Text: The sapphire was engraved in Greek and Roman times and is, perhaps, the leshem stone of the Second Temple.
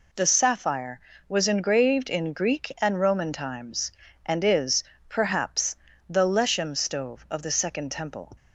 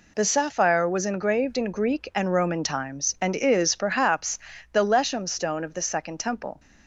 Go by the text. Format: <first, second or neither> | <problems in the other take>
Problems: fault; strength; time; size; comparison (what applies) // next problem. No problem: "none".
second | says "stove" for "stone"; at 6.7 s